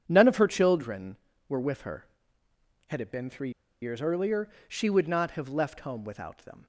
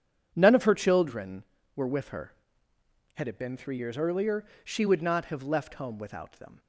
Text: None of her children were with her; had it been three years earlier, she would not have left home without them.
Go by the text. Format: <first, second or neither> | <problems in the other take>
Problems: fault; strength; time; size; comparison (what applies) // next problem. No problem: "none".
second | pauses between "three" and "years"; slight; at 3.4 s; 0.32 s long